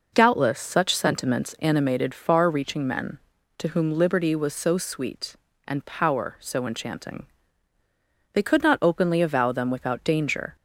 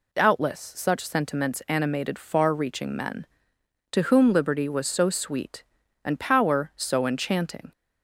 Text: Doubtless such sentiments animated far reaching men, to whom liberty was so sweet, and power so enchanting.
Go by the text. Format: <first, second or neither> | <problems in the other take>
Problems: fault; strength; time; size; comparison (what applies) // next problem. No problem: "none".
second | goes on to say "They could not openly avow them without danger"; strong; from 8.3 s on; 2.2 s long